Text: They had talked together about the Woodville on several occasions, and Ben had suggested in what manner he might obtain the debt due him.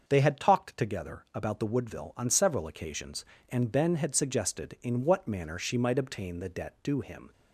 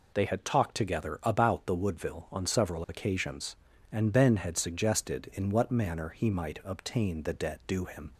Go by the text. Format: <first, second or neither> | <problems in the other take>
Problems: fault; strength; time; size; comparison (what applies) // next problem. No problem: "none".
second | starts louder than the rest; until 1.0 s; 6.5 dB // says "she" for "he"; at 5.5 s